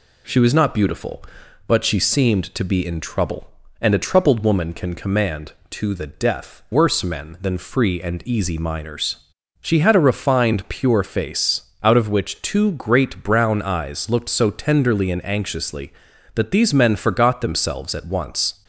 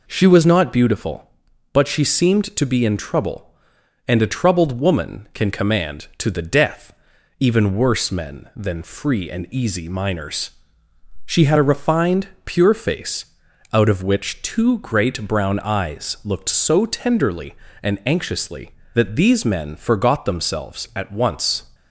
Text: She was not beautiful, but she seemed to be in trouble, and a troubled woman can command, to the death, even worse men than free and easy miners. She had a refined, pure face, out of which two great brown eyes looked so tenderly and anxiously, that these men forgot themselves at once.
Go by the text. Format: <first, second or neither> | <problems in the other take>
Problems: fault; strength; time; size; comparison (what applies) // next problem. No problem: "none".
second | skips "even"; at 6.6 s